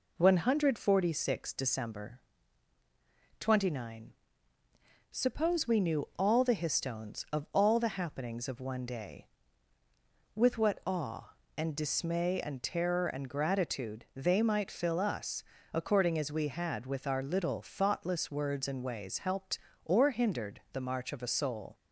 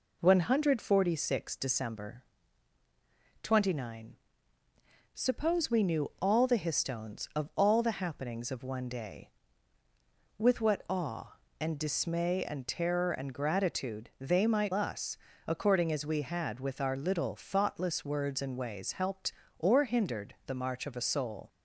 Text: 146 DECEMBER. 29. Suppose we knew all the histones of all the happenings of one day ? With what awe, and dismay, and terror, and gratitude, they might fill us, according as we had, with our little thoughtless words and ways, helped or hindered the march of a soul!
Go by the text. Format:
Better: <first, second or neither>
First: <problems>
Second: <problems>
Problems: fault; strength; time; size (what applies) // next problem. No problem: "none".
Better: first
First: none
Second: skips "fill"; at 14.7 s